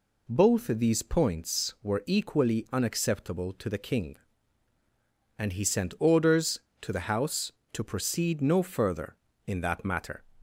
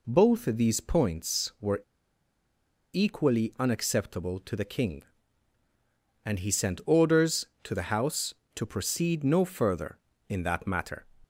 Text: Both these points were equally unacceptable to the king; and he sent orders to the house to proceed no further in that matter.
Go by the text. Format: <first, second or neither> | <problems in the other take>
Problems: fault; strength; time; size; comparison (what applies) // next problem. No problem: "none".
first | pauses between "were" and "equally"; at 1.7 s; 1.1 s long